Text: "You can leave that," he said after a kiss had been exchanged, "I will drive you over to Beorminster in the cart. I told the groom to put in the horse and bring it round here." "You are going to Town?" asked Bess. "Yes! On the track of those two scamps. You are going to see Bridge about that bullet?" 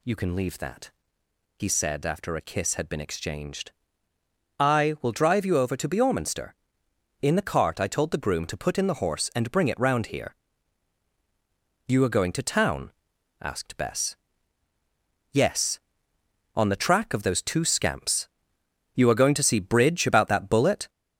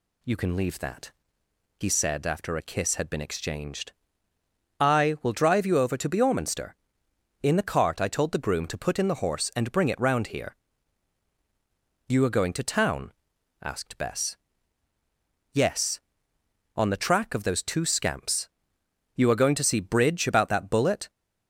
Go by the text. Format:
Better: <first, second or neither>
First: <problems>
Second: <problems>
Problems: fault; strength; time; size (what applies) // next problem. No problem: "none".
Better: second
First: gets louder; noticeable; throughout; 4.5 dB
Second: none